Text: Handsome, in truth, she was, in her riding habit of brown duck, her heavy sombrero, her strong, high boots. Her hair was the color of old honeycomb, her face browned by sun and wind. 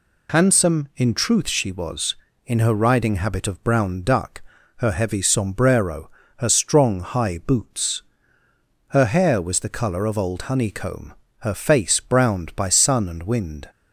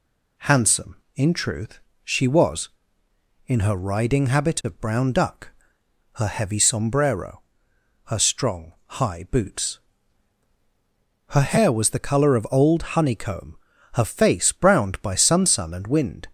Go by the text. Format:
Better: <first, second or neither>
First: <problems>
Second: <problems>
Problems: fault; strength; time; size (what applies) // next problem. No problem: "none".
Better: first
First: none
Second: says "sun" twice; at 15.4 s